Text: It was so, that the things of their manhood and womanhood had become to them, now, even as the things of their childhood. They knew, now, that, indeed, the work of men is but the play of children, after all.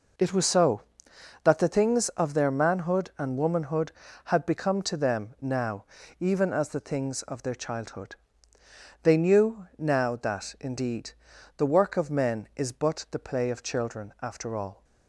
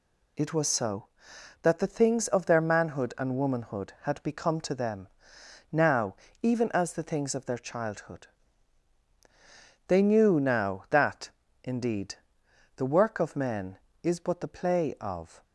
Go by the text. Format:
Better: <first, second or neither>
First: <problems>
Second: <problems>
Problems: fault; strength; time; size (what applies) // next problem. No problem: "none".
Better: first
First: none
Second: stops before "children after all"; at 15.4 s